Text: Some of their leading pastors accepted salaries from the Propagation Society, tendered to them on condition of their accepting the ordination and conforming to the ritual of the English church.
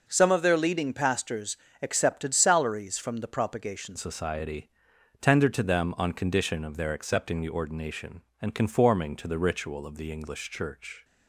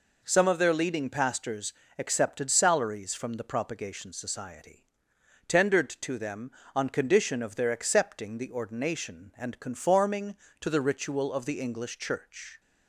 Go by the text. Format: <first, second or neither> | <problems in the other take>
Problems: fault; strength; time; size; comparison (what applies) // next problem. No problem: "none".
second | pauses between "pastors" and "accepted"; slight; at 1.5 s; 0.24 s long; slight in the second // changes voice at "Society"; from 3.9 s on; 7.1 s long